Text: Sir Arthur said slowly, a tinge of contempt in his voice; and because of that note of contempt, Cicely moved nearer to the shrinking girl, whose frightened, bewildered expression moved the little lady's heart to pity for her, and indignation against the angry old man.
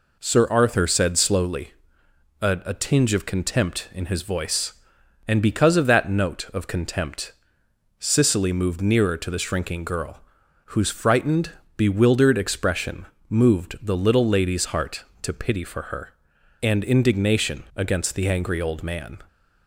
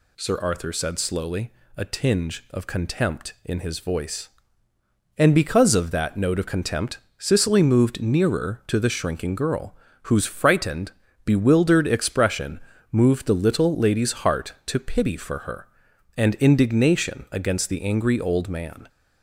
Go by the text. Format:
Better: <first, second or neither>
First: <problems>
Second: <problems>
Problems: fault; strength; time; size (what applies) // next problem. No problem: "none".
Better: second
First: says "a" twice; at 2.6 s // pauses between "expression" and "moved"; slight; at 13.0 s; 0.24 s long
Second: pauses between "expression" and "moved"; slight; at 12.5 s; 0.32 s long